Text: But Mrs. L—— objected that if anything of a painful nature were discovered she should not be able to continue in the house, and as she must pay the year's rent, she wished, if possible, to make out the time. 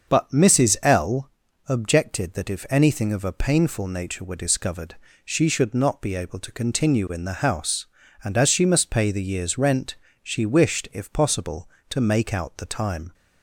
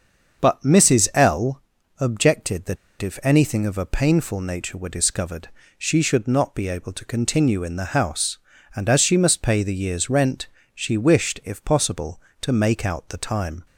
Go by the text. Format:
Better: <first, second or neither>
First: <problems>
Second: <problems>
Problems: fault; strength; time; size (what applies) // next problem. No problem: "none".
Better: first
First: starts louder than the rest; until 1.1 s; 6.5 dB // pauses between "discovered" and "she"; slight; at 4.9 s; 0.30 s long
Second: starts louder than the rest; until 1.4 s; 6.5 dB // pauses between "that" and "if"; slight; at 2.7 s; 0.24 s long // pauses between "discovered" and "she"; slight; at 5.4 s; 0.30 s long